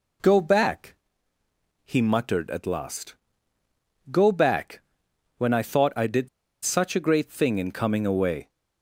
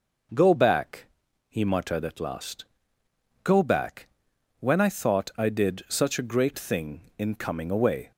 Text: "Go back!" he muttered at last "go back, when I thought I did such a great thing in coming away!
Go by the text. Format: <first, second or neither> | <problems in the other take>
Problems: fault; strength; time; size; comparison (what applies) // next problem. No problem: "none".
second | pauses between "last" and "go"; noticeable; at 3.1 s; 0.96 s long; noticeable in the second // pauses between "did" and "such"; at 6.2 s; 0.36 s long